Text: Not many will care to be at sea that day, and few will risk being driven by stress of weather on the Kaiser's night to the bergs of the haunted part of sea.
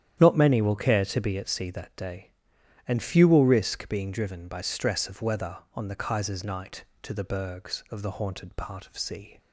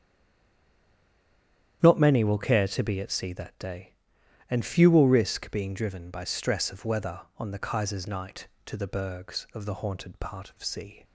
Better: first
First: starts louder than the rest; strong; until 1.2 s; 10 dB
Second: stays silent before the first word; noticeable; until 1.8 s; 1.8 s long // starts louder than the rest; strong; until 2.8 s; 10 dB

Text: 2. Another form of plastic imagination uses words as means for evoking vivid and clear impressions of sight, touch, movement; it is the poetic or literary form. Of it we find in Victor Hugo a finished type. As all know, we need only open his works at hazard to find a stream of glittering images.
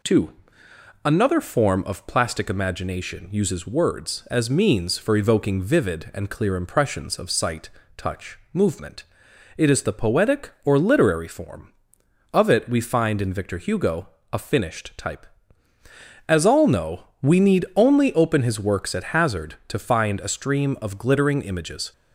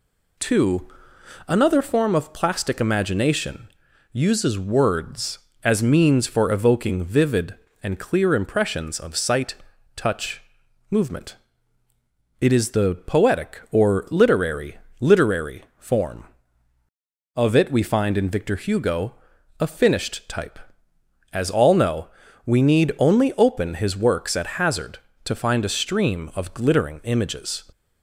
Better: first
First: pauses between "Hugo" and "a"; slight; at 14.0 s; 0.24 s long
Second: pauses between "imagination" and "uses"; at 3.6 s; 0.44 s long // says "literary" twice; at 14.9 s // pauses between "Hugo" and "a"; at 19.1 s; 0.44 s long

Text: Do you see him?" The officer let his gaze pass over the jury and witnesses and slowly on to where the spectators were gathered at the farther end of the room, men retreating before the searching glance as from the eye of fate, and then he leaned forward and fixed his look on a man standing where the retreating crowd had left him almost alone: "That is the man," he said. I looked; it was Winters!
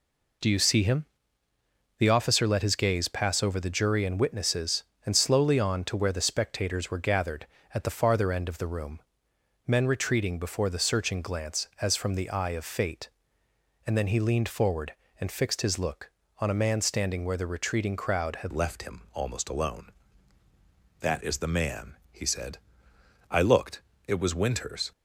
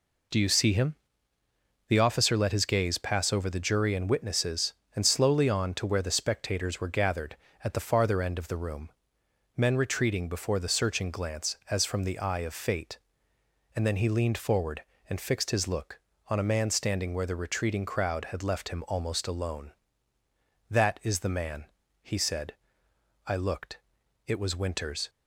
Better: second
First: changes voice at "left"; from 18.5 s on; 6.4 s long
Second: none

